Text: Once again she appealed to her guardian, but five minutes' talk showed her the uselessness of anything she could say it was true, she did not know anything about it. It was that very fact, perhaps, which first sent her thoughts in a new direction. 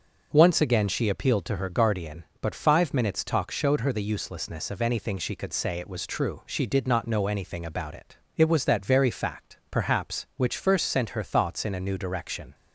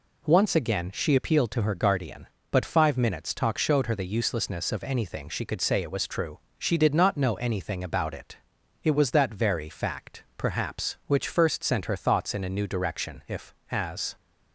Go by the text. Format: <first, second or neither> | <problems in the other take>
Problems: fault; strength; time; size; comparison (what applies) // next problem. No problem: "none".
first | goes on to say "If as"; noticeable; from 13.2 s on; 0.88 s long